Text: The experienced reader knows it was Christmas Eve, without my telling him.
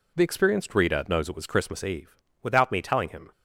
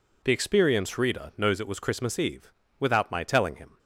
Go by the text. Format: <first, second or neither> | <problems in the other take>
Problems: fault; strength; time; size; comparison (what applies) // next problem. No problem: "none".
second | says "me" for "my"; at 2.7 s